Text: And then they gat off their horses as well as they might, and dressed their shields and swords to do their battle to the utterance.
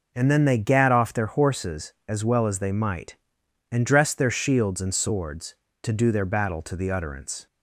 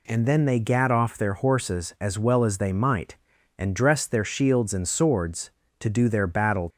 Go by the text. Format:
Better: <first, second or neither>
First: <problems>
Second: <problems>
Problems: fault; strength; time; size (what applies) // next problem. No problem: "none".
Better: first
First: none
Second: stops before "to the utterance"; at 6.7 s